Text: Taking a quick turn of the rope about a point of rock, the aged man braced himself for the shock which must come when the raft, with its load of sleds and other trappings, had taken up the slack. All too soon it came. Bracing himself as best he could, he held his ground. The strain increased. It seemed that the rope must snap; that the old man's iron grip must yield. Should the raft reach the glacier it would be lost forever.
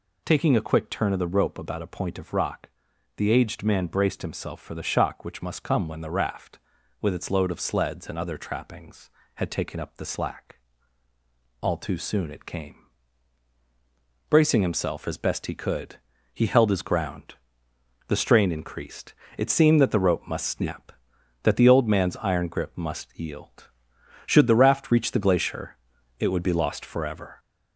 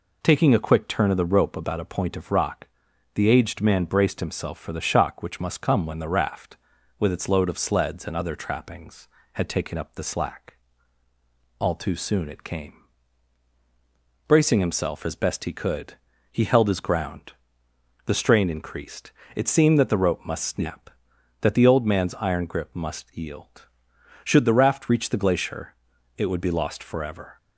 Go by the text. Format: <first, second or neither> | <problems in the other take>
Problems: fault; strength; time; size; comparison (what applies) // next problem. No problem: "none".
second | gets louder; slight; throughout; 2.5 dB // pauses between "glacier" and "it"; at 25.7 s; 0.42 s long; also in the second